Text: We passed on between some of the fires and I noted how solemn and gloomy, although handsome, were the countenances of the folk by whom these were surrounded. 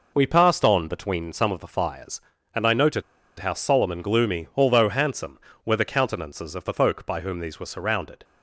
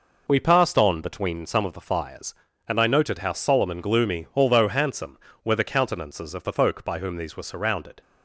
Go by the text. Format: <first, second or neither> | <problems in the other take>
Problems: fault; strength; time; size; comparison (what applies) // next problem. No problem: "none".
second | pauses between "noted" and "how"; at 3.0 s; 0.37 s long